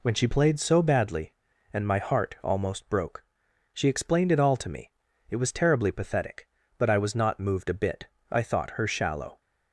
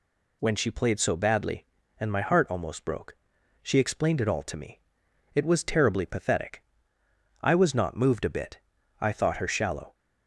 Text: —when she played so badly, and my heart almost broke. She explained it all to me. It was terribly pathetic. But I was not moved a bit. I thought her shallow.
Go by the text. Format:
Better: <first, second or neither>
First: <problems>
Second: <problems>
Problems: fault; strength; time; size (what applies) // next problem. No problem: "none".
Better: first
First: none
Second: skips "But"; at 7.0 s